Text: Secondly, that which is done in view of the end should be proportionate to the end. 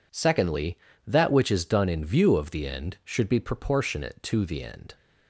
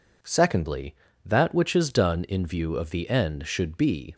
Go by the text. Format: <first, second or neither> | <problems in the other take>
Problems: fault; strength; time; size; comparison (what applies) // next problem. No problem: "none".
first | stops before "proportionate to the end"; at 4.1 s